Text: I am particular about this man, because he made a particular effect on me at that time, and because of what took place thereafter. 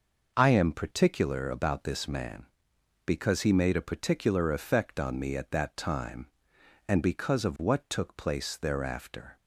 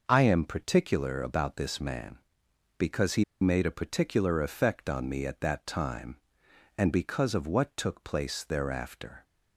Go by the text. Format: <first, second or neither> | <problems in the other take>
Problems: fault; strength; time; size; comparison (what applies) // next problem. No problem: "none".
first | pauses between "he" and "made"; slight; at 3.2 s; 0.17 s long